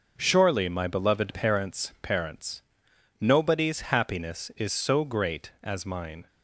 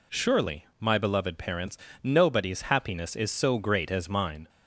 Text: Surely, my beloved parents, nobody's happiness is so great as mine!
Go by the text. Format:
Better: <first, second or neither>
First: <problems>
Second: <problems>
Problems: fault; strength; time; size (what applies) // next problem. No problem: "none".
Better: second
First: says "parents" twice; at 2.0 s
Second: none